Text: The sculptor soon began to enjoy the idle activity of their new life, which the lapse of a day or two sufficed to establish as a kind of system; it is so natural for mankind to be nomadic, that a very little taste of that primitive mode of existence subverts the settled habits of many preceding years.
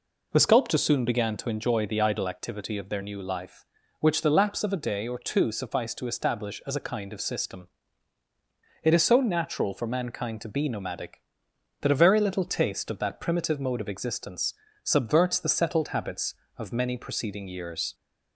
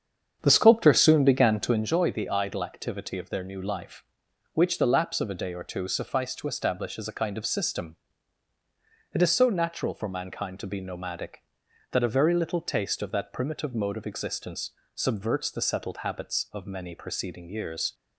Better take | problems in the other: first | starts louder than the rest; strong; until 1.9 s; 8 dB // pauses between "existence" and "subverts"; slight; at 14.7 s; 0.24 s long; slight in the first

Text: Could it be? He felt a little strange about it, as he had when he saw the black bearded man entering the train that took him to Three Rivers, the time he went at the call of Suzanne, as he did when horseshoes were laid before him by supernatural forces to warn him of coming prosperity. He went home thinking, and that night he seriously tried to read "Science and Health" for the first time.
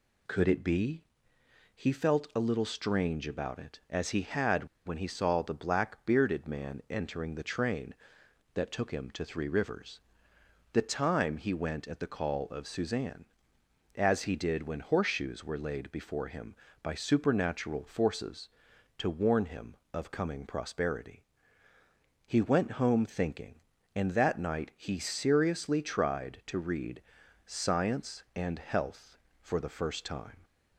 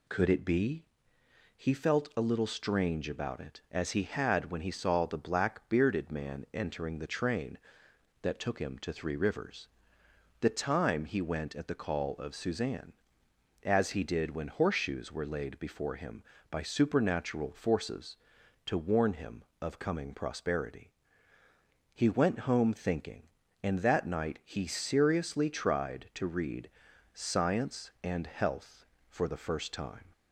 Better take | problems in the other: second | pauses between "had" and "when"; slight; at 4.6 s; 0.18 s long // pauses between "read" and "Science"; at 27.0 s; 0.42 s long; also in the second

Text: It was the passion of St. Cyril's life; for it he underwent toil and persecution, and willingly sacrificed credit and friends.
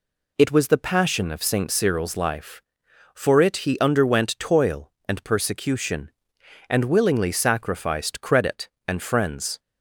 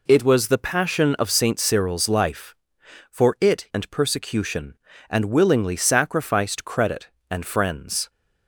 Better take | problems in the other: first | skips "he underwent toil"; at 3.6 s

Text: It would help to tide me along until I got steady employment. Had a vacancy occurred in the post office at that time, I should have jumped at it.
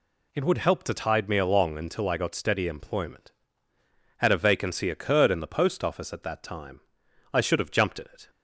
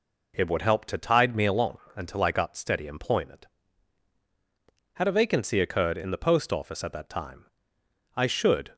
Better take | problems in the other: first | pauses between "along" and "until"; slight; at 1.7 s; 0.18 s long // stops before "have jumped at it"; at 8.7 s

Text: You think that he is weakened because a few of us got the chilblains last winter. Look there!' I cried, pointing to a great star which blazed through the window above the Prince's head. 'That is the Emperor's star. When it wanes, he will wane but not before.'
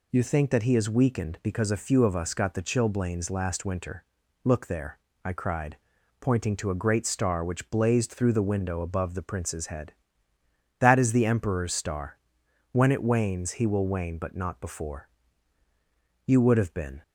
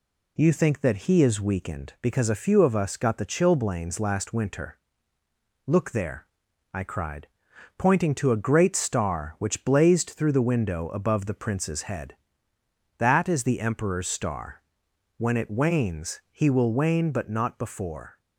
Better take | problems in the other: second | goes on to say "You would have been"; noticeable; from 16.2 s on; 0.76 s long

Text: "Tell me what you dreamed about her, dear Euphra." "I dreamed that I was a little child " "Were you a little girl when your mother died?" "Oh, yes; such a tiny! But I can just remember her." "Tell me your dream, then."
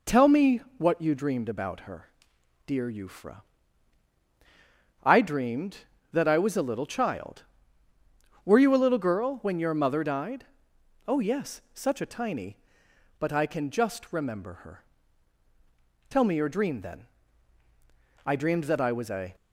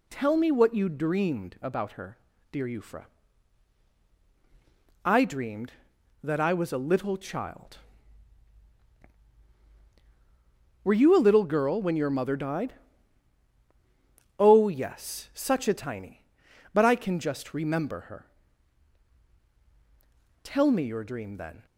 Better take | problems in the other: second | pauses between "me" and "what"; slight; at 0.6 s; 0.16 s long // goes on to say "I dreamed that I was a"; noticeable; from 18.2 s on; 1.0 s long

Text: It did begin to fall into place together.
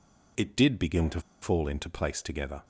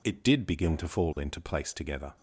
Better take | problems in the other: second | pauses between "to" and "fall"; slight; at 1.2 s; 0.20 s long

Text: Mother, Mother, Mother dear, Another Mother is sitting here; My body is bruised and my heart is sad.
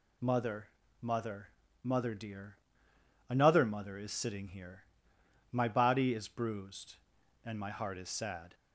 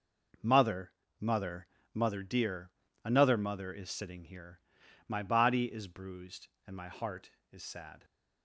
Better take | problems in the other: neither | none

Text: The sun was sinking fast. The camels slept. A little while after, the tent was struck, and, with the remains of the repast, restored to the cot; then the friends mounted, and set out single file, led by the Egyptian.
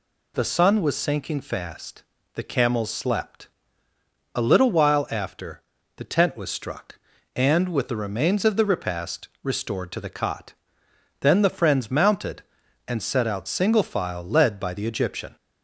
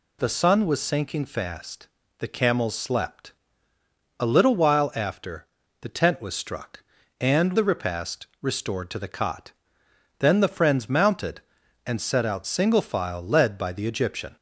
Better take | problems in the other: first | skips "with the remains of"; at 7.5 s

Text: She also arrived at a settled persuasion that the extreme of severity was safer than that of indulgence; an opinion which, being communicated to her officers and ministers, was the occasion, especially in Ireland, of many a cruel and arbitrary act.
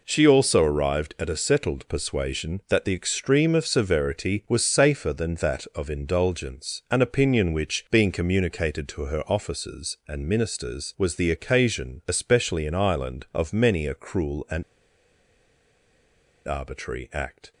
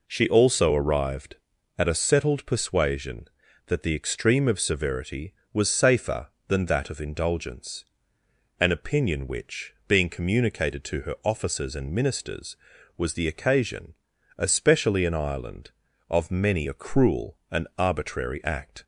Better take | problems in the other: second | pauses between "and" and "arbitrary"; strong; at 14.6 s; 1.8 s long

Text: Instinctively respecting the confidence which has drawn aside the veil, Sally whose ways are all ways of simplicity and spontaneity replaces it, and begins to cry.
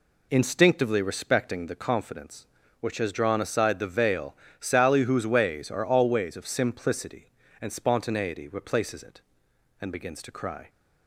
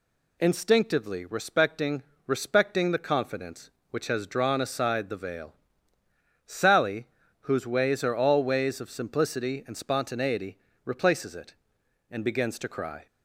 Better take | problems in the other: first | says "respecting" twice; at 2.2 s // pauses between "Sally" and "whose"; slight; at 7.0 s; 0.36 s long // pauses between "spontaneity" and "replaces"; slight; at 10.5 s; 0.26 s long

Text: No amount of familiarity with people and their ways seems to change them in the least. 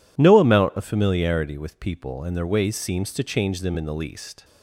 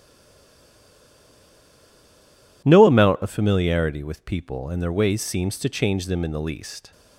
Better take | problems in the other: first | stays silent before the first word; strong; until 2.6 s; 2.6 s long

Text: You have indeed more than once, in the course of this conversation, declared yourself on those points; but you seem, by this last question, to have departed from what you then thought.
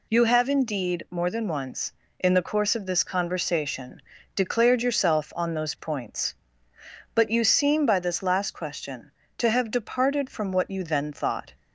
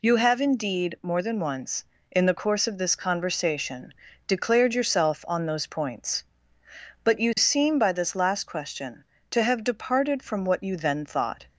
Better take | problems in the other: neither | none

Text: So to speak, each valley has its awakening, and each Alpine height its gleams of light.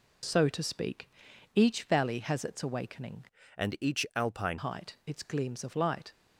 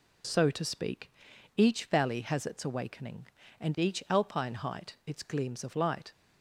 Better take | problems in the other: second | changes voice from "and" to "Alpine"; from 3.5 to 4.5 s; 1.0 s long

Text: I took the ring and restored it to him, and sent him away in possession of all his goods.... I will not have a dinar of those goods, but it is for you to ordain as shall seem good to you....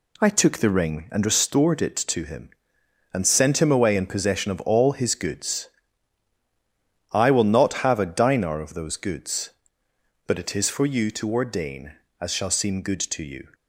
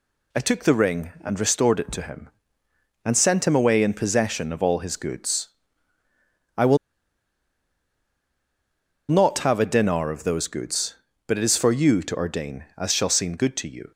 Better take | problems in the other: first | pauses between "will" and "not"; strong; at 6.7 s; 2.3 s long

